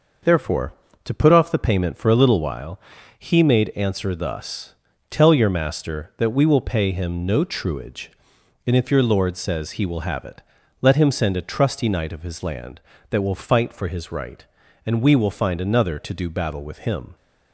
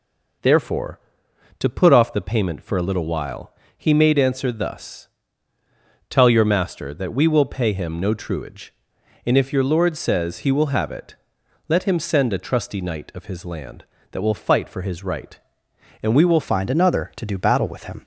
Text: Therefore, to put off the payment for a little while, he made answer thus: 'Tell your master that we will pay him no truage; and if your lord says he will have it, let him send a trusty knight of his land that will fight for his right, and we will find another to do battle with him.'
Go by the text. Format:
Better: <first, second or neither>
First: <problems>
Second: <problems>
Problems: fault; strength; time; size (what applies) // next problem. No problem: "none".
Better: first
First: none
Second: changes voice at "find"; from 16.4 s on; 1.6 s long